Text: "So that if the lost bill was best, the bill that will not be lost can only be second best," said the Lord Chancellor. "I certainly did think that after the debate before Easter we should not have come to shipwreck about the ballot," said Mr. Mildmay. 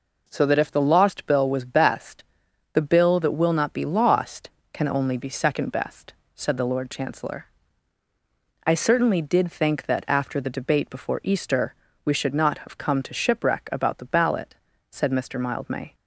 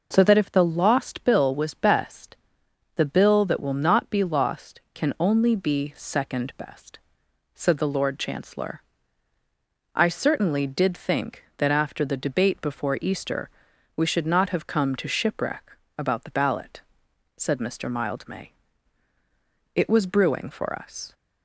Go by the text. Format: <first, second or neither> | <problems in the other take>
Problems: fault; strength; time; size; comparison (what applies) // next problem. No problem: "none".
first | pauses between "Easter" and "we"; noticeable; at 13.4 s; 0.48 s long; slight in the first // pauses between "shipwreck" and "about"; slight; at 15.6 s; 0.36 s long // goes on to say "It was brewing for us"; from 19.7 s on; 1.3 s long